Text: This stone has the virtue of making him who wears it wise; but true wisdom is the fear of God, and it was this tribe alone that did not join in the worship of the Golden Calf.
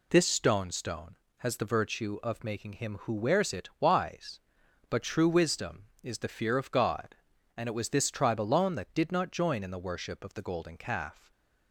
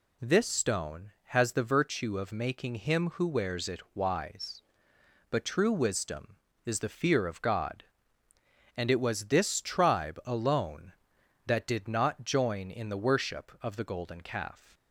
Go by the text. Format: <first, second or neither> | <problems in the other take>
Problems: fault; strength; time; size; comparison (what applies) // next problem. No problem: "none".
second | says "stone" twice; at 0.7 s // stays silent after the last word; slight; from 11.1 s on; 0.6 s long